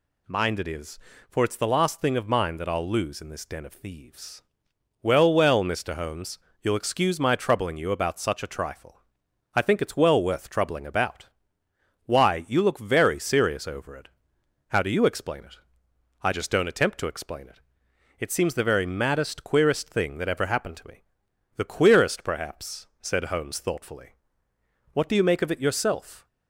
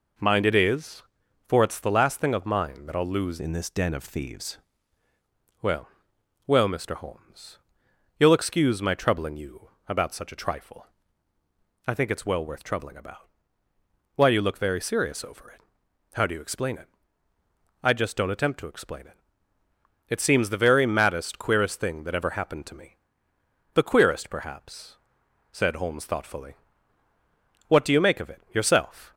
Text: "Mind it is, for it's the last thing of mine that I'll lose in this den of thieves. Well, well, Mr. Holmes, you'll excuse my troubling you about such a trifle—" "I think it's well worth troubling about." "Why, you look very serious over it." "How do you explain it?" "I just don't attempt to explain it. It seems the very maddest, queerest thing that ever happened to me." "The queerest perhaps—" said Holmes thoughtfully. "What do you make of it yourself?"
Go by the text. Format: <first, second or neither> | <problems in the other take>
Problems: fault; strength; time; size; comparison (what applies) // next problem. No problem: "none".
first | changes voice from "in" to "thieves"; from 3.3 to 4.5 s; 1.2 s long // pauses between "you" and "about"; slight; at 9.6 s; 0.20 s long